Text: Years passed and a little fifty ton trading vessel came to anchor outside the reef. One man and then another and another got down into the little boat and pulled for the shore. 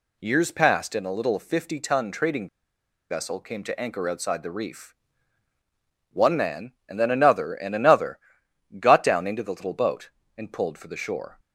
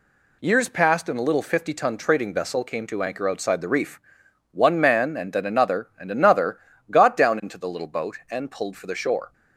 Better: second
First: pauses between "trading" and "vessel"; noticeable; at 2.4 s; 0.62 s long // pauses between "another" and "got"; noticeable; at 8.1 s; 0.60 s long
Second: pauses between "another" and "got"; slight; at 6.5 s; 0.30 s long

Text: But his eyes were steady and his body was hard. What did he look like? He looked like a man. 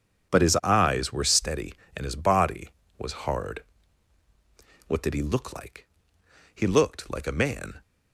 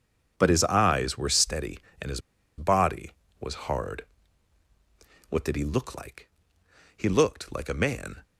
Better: first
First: starts louder than the rest; strong; until 1.3 s; 7.5 dB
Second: starts louder than the rest; strong; until 1.3 s; 7.5 dB // pauses between "his" and "body"; at 2.2 s; 0.37 s long

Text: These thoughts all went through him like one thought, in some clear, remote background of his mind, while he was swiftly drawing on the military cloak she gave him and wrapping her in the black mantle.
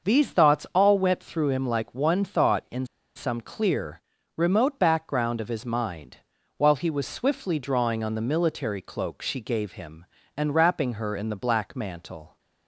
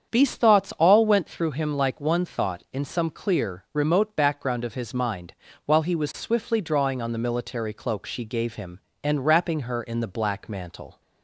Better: second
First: starts louder than the rest; until 1.1 s; 6.5 dB // pauses between "in" and "some"; slight; at 2.8 s; 0.30 s long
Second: starts louder than the rest; strong; until 1.1 s; 8 dB

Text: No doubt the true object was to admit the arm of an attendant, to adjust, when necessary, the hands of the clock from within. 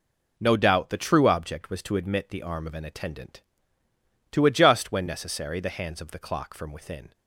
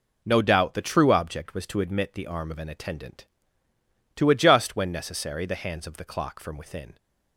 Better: neither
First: none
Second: none

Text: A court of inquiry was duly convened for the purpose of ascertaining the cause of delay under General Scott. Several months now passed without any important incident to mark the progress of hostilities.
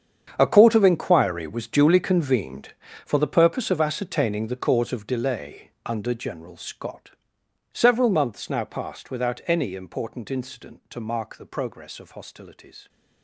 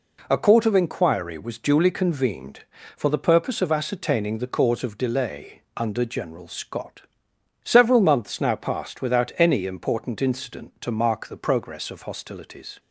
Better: second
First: gets quieter; strong; throughout; 16 dB // pauses between "delay" and "under"; slight; at 5.7 s; 0.16 s long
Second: pauses between "delay" and "under"; slight; at 5.6 s; 0.16 s long

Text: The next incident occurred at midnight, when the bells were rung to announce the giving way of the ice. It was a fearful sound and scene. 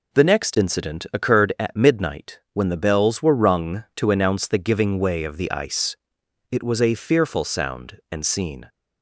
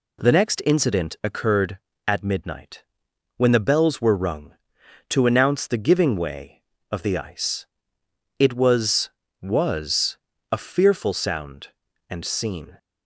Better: first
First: none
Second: says "was" twice; at 9.4 s

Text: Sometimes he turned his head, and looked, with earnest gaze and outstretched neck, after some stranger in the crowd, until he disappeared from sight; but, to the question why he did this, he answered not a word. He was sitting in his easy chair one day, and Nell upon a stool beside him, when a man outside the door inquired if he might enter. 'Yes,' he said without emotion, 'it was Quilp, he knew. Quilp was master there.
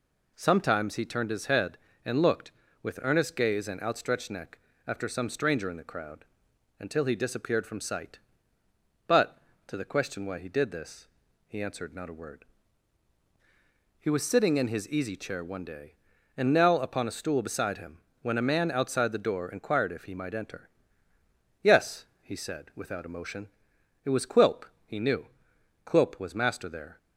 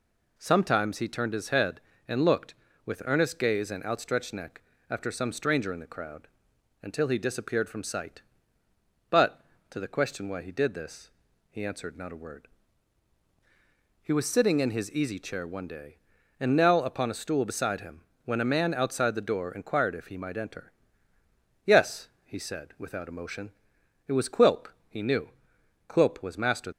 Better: first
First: none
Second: stops before "there"; at 26.7 s

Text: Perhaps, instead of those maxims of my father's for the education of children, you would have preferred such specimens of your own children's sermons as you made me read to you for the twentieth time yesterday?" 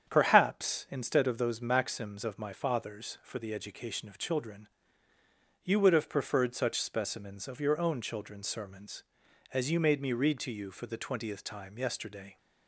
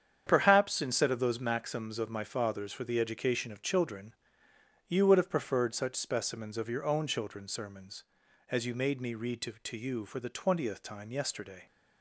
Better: first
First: starts louder than the rest; strong; until 1.1 s; 8 dB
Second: starts louder than the rest; strong; until 1.2 s; 8 dB // says "to" twice; at 9.6 s

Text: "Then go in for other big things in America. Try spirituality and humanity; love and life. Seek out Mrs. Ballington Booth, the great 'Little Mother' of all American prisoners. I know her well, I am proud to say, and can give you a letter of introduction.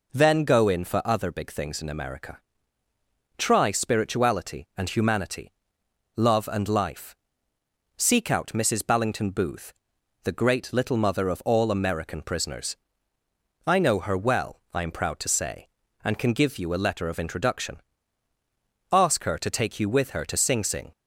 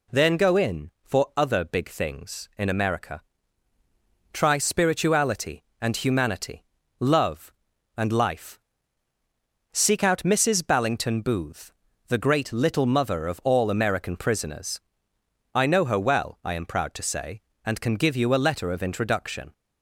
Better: second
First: goes on to say "Ask her to take you with her to Sing Sing"; strong; from 18.9 s on; 2.0 s long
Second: none

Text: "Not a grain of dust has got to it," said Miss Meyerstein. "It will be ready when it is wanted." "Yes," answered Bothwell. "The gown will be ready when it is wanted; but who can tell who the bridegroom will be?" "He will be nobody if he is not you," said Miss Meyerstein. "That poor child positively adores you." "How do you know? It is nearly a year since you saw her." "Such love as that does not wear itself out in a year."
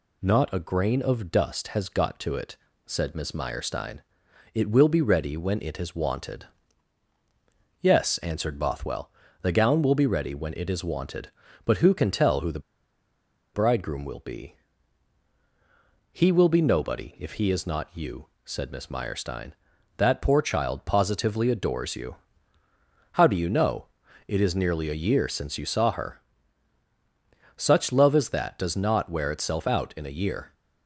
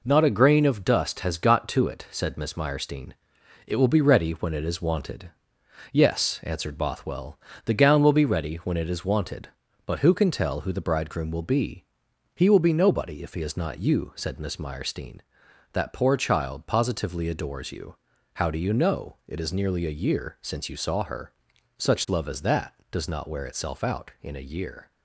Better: second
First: pauses between "the" and "bridegroom"; noticeable; at 12.5 s; 0.95 s long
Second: none

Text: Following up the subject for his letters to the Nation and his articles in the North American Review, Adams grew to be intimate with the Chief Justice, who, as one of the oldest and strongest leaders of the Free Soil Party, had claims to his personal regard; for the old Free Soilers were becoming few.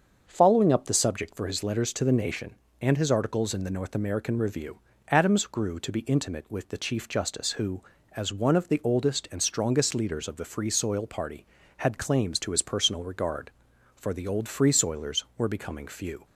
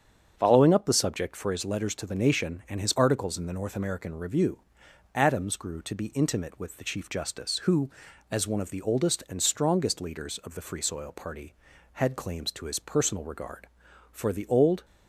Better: first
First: starts louder than the rest; until 1.2 s; 7 dB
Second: starts louder than the rest; strong; until 1.3 s; 7.5 dB // stops before "Free Soilers were becoming few"; at 14.8 s

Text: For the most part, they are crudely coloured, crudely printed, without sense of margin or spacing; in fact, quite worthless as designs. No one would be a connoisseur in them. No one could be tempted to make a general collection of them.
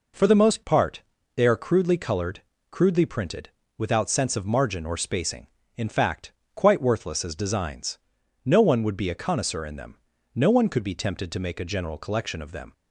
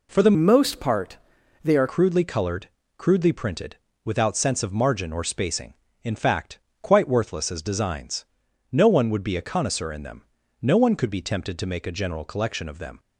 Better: first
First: none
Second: changes voice from "most" to "are"; from 0.3 to 1.8 s; 1.5 s long

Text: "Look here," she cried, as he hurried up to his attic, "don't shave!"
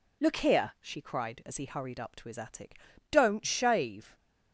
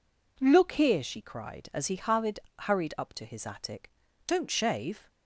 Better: first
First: none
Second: says "hurried" twice; at 2.5 s

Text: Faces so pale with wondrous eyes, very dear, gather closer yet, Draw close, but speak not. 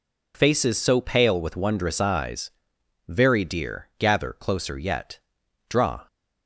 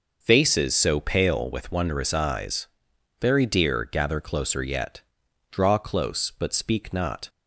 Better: second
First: stops before "close but speak not"; at 6.0 s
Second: none

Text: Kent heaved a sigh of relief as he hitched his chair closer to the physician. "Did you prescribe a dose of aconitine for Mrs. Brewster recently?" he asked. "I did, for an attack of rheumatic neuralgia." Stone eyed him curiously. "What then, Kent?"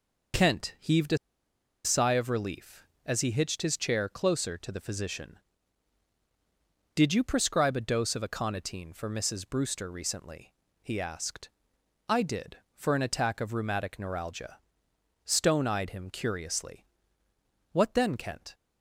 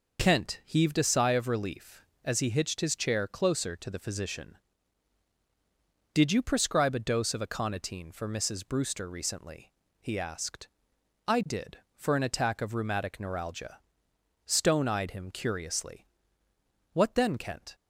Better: second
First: pauses between "a" and "sigh"; noticeable; at 1.1 s; 0.67 s long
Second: none

